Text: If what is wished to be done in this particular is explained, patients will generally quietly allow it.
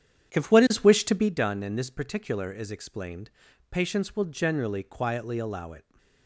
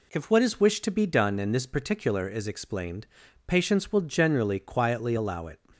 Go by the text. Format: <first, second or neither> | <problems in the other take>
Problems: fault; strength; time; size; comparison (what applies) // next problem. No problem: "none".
second | starts louder than the rest; strong; until 1.3 s; 8.5 dB